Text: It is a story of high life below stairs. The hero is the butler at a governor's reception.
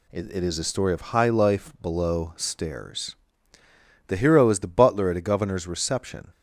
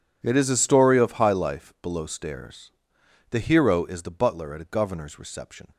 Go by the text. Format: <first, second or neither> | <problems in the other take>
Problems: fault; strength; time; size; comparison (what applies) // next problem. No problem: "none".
second | says "It" twice; at 0.3 s